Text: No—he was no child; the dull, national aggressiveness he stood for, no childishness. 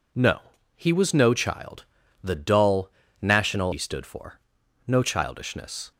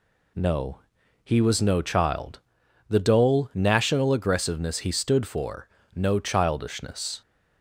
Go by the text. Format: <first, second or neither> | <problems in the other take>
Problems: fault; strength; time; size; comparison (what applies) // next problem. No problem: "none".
second | skips "aggressiveness"; at 3.7 s